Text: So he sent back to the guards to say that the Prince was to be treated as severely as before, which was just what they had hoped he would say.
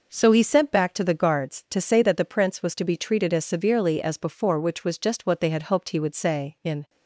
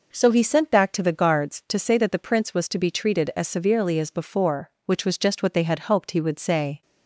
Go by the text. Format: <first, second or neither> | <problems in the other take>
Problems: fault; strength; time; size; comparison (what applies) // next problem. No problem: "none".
second | goes on to say "In"; slight; from 6.6 s on; 0.26 s long